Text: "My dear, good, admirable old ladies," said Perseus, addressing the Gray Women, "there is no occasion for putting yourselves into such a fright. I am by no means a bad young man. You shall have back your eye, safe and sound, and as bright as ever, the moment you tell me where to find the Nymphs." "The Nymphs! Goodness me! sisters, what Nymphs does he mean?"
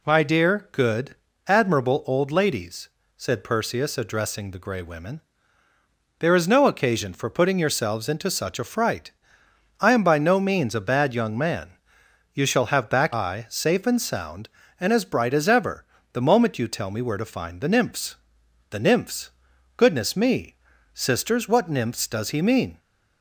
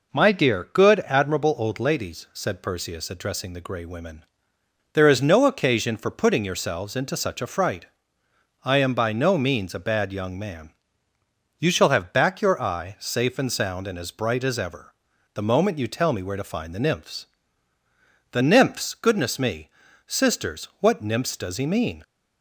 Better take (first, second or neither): second